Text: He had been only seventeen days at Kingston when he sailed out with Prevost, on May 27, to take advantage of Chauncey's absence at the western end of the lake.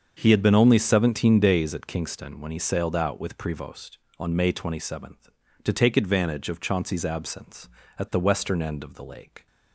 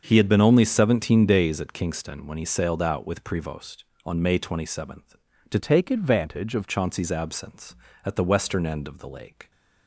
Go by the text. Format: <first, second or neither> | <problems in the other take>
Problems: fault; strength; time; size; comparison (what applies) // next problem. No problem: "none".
first | starts louder than the rest; until 1.0 s; 6.5 dB; also in the first // changes voice from "take" to "of"; from 5.5 to 6.6 s; 1.1 s long